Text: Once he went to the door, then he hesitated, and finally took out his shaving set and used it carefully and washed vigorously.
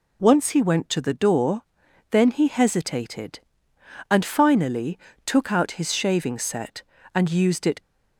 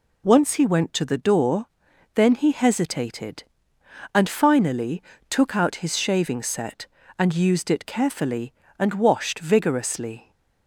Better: second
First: pauses between "finally" and "took"; slight; at 4.9 s; 0.26 s long // stops before "carefully and washed vigorously"; at 7.8 s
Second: pauses between "finally" and "took"; slight; at 5.0 s; 0.26 s long

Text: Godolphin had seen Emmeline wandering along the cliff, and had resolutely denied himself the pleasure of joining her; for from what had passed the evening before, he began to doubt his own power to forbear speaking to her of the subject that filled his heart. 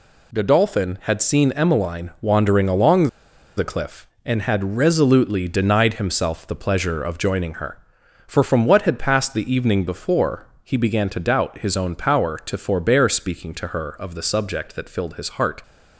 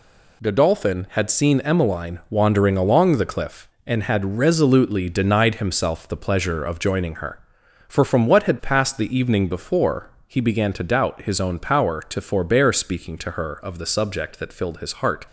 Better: second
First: pauses between "along" and "the"; noticeable; at 3.0 s; 0.48 s long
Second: none

